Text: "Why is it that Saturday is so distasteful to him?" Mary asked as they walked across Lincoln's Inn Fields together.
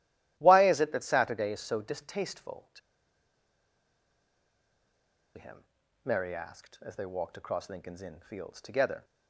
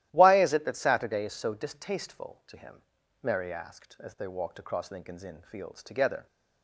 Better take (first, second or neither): second